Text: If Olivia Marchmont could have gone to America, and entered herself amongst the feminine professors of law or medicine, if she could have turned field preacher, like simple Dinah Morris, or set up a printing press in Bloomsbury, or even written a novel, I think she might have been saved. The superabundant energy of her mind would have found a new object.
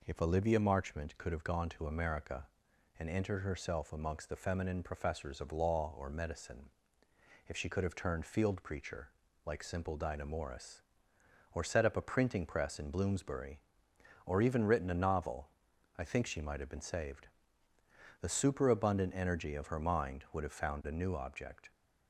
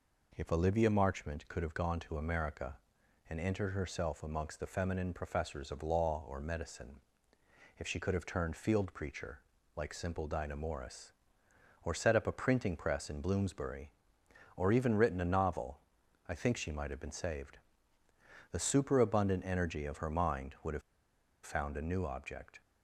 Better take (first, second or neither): first